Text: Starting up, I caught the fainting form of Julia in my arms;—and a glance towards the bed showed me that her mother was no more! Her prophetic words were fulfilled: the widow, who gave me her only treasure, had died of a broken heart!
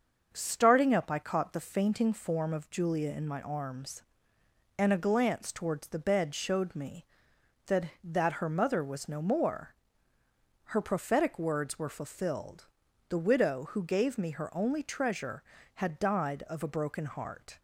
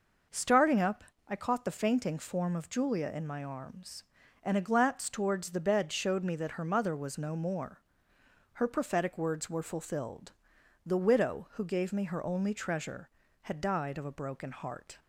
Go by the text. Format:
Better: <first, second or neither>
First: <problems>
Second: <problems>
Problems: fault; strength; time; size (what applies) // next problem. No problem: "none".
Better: second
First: starts louder than the rest; until 1.3 s; 6.5 dB // says "that" twice; at 8.0 s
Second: none